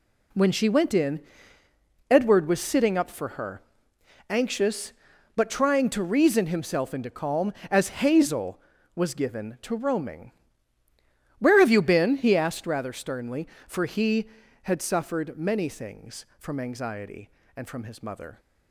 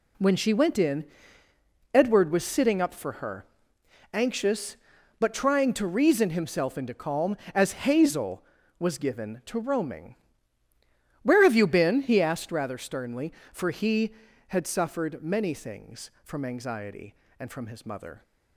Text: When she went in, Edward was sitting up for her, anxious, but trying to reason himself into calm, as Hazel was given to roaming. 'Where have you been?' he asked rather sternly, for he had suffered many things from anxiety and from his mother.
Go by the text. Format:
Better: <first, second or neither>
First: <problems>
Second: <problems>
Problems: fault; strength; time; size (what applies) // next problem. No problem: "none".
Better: neither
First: none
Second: none